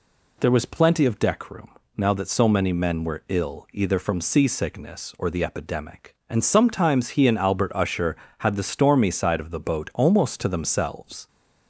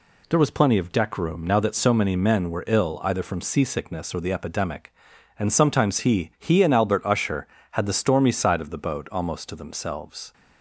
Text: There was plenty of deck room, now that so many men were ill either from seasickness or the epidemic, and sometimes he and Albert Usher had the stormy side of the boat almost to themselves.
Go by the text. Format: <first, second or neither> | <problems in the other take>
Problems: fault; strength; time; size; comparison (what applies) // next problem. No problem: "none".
first | says "he" twice; at 6.3 s